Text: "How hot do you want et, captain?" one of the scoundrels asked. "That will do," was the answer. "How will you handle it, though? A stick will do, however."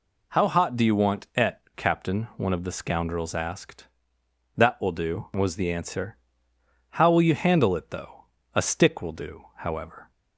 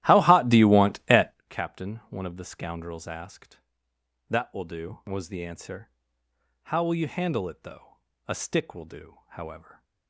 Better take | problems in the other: first | starts louder than the rest; strong; until 1.4 s; 14.5 dB

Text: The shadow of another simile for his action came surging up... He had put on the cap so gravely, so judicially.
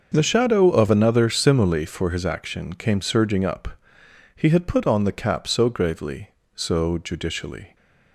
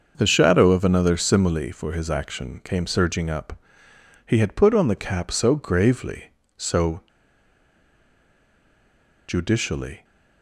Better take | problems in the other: first | starts louder than the rest; until 1.1 s; 6 dB; noticeable in the first // pauses between "so" and "judicially"; strong; at 7.0 s; 2.2 s long

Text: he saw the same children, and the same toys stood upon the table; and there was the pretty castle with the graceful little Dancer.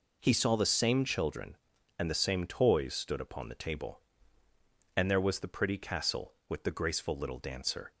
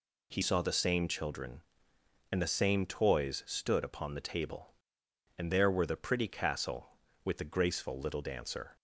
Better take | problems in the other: first | says "were" for "was"; at 5.7 s

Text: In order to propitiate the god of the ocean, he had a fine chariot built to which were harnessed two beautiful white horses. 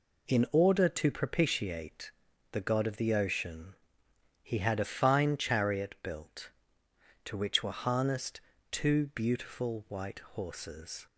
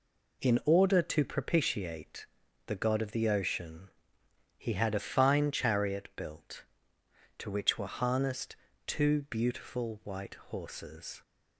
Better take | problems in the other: neither | pauses between "propitiate" and "the"; the same in both // pauses between "harnessed" and "two"; slight; the same in both

